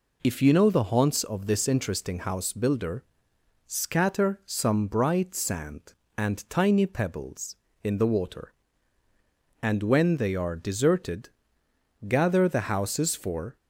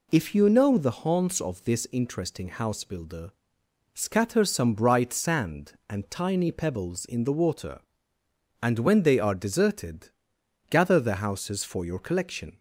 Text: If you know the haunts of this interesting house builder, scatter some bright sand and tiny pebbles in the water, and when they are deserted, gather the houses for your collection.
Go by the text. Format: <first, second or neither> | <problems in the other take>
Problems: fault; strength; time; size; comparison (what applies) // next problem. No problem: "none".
second | stops before "your collection"; at 13.5 s